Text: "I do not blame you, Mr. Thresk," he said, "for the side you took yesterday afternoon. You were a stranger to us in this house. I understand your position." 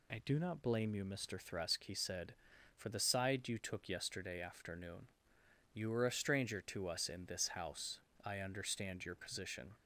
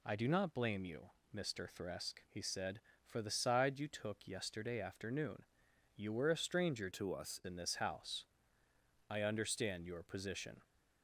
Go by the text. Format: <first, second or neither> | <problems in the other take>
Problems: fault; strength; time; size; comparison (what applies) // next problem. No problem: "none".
first | changes voice from "to" to "us"; from 6.9 to 7.3 s; 0.4 s long